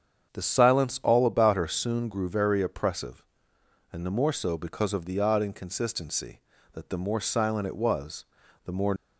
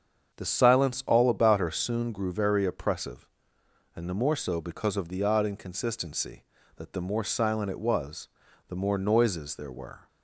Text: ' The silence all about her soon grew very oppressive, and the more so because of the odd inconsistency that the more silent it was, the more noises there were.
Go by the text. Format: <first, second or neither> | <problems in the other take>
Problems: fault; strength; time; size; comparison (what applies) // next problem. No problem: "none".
second | starts louder than the rest; strong; until 1.3 s; 7.5 dB; strong in the second // stops before "noises there were"; at 8.9 s